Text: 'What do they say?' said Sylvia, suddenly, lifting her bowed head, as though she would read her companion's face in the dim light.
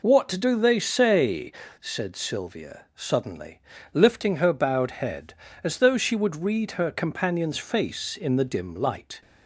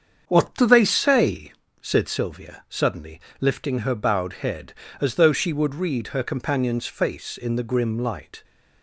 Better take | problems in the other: first | starts louder than the rest; strong; until 1.3 s; 7.5 dB // says "grim" for "dim"; at 7.6 s

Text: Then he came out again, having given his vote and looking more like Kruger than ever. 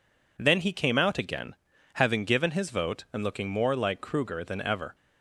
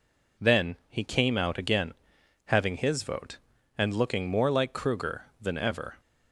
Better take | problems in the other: first | skips "given"; at 2.7 s

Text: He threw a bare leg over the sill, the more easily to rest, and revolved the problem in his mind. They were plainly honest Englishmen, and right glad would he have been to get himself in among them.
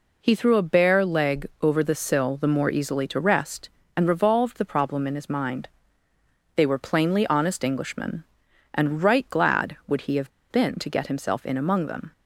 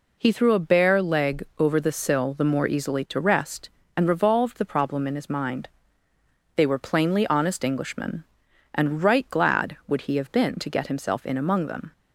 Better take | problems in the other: second | pauses between "have" and "been"; slight; at 10.2 s; 0.20 s long

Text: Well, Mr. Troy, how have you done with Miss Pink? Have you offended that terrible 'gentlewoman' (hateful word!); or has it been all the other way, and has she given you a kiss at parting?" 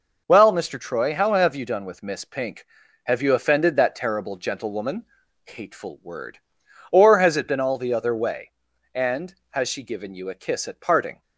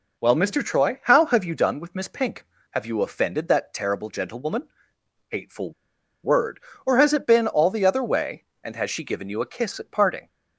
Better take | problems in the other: first | pauses between "hateful" and "word"; noticeable; at 5.7 s; 0.52 s long

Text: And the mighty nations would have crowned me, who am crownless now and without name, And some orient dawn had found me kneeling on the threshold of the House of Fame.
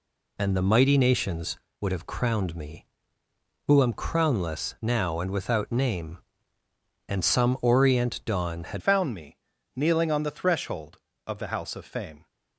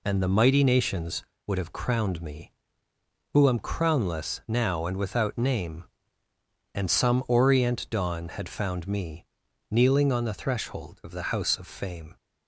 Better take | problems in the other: second | changes voice at "found"; from 8.7 s on; 3.5 s long // pauses between "me" and "kneeling"; at 9.3 s; 0.38 s long; also in the second

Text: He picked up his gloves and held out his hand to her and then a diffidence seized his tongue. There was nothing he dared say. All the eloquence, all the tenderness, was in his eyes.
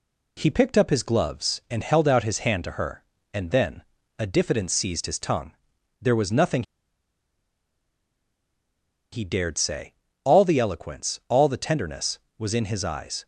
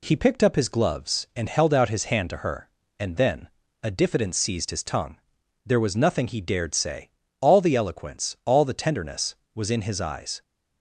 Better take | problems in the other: second | pauses between "then" and "a"; at 3.8 s; 0.38 s long; also in the second // pauses between "nothing" and "he"; strong; at 6.6 s; 2.5 s long

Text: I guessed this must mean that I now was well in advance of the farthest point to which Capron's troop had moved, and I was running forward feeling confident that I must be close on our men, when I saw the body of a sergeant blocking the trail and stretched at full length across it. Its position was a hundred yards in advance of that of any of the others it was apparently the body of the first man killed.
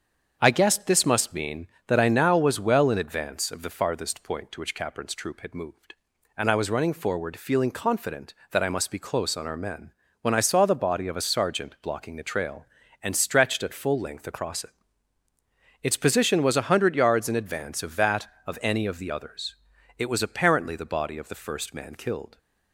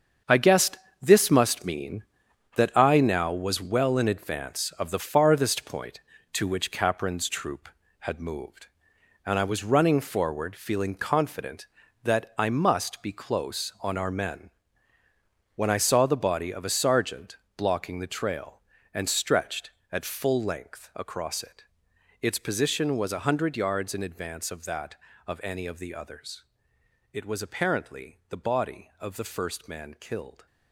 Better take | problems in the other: first | gets quieter; strong; throughout; 9.5 dB // starts louder than the rest; until 1.5 s; 7 dB; strong in the first // pauses between "guessed" and "this"; slight; at 0.7 s; 0.24 s long // pauses between "sergeant" and "blocking"; slight; at 17.3 s; 0.22 s long // pauses between "others" and "it"; noticeable; at 26.4 s; 0.68 s long; also in the first

